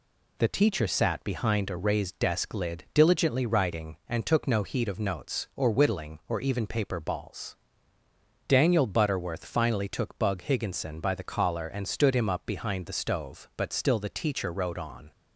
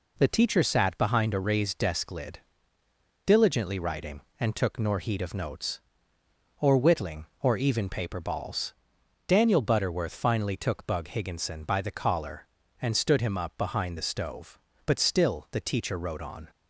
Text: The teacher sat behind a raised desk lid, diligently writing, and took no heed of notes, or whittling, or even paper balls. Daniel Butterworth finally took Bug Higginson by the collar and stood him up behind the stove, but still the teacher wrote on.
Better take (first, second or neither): first